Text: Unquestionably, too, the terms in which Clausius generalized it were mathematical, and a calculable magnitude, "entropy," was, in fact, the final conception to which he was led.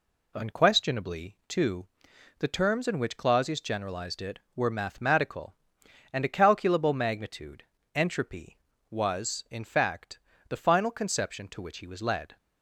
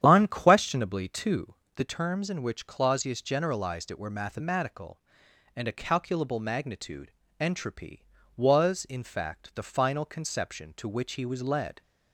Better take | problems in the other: first | starts louder than the rest; strong; until 1.9 s; 9.5 dB

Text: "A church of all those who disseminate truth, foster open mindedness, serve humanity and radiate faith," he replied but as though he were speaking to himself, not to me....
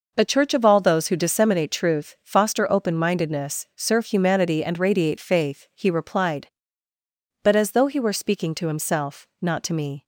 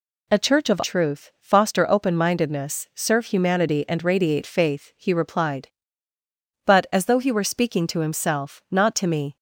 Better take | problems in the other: first | skips "all those who disseminate"; at 0.8 s

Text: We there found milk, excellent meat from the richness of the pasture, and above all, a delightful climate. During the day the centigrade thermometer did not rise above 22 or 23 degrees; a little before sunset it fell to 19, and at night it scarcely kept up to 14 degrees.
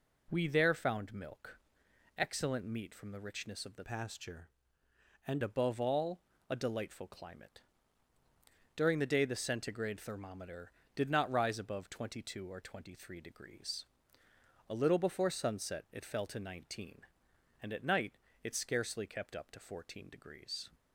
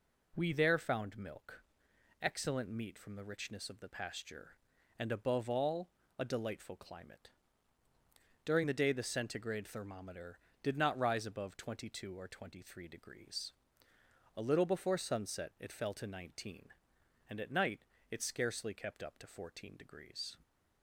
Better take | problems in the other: second | changes voice from "pasture" to "and"; from 3.8 to 5.4 s; 1.6 s long // pauses between "night" and "it"; slight; at 18.1 s; 0.30 s long; slight in the second

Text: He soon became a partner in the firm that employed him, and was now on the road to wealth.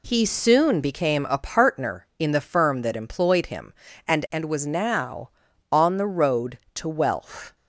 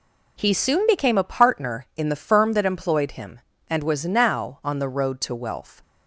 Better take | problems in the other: second | says "and" twice; at 4.3 s

